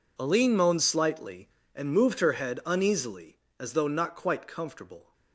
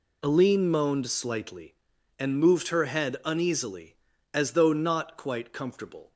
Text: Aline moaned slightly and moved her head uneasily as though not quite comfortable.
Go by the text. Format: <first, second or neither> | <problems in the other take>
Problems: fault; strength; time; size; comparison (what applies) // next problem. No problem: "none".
neither | none